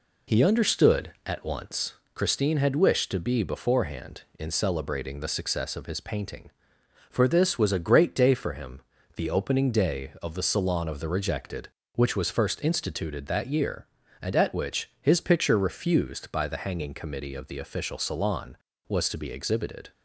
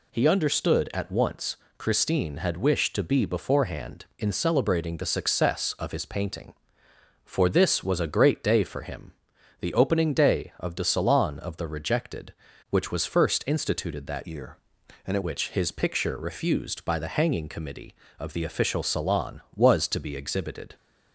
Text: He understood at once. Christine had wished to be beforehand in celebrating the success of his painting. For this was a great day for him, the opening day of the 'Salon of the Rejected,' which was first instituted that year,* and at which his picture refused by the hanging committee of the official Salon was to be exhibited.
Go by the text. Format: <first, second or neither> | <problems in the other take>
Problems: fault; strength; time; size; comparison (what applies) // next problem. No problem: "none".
first | changes voice from "year" to "at"; from 14.2 to 15.2 s; 1.0 s long